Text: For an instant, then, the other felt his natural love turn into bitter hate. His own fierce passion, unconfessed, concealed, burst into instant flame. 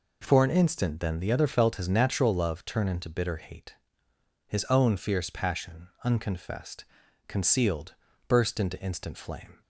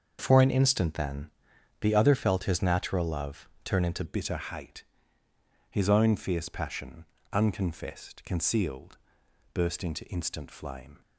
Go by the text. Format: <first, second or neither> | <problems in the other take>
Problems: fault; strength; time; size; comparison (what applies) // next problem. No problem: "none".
first | starts louder than the rest; until 1.2 s; 6.5 dB // pauses between "love" and "turn"; slight; at 3.4 s; 0.16 s long // changes voice at "bitter"; from 4.0 s on; 7.0 s long